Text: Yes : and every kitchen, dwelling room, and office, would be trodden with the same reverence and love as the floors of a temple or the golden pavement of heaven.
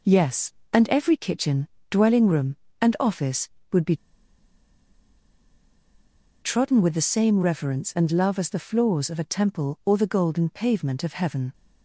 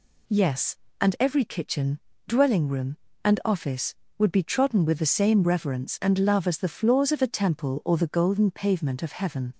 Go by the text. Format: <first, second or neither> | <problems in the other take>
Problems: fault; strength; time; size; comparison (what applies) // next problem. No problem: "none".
second | pauses between "be" and "trodden"; strong; at 3.9 s; 2.4 s long